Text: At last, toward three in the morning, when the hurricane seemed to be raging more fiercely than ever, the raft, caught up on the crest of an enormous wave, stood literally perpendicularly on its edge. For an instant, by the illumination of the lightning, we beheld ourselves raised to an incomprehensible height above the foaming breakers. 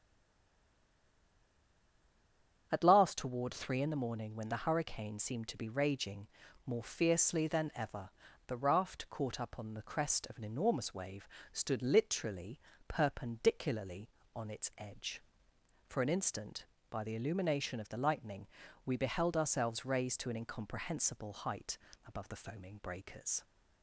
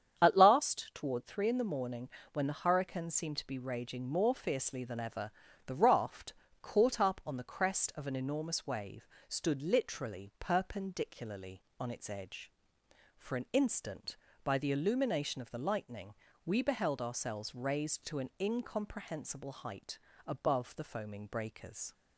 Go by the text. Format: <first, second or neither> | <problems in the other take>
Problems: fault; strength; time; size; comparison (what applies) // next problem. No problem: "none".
second | stays silent before the first word; strong; until 2.6 s; 2.6 s long // starts louder than the rest; strong; until 3.7 s; 8 dB; strong in the second // pauses between "raging" and "more"; at 6.2 s; 0.38 s long // pauses between "literally" and "perpendicularly"; slight; at 12.5 s; 0.30 s long // pauses between "height" and "above"; slight; at 21.7 s; 0.28 s long; slight in the second